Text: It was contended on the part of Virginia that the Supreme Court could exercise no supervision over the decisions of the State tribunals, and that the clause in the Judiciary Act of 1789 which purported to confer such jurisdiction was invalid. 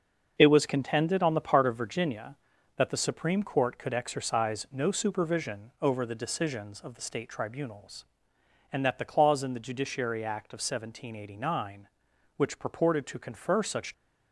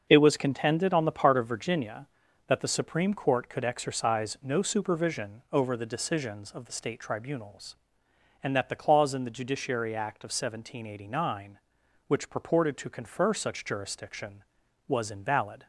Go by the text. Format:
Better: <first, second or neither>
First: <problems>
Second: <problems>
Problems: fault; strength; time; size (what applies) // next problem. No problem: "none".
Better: second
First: starts louder than the rest; until 1.3 s; 6.5 dB // stops before "jurisdiction was invalid"; at 13.9 s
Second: starts louder than the rest; until 1.0 s; 6.5 dB